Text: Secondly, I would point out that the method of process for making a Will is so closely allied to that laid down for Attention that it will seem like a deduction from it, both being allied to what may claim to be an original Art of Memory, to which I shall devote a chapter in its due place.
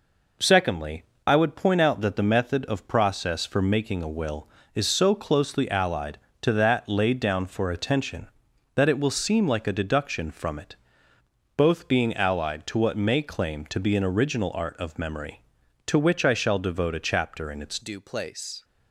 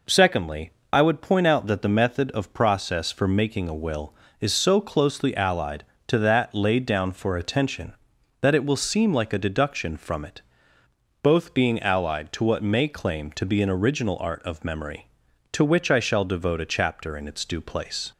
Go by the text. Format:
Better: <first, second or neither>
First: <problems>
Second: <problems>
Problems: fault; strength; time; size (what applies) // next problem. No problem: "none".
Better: second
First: changes voice at "due"; from 17.8 s on; 0.8 s long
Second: none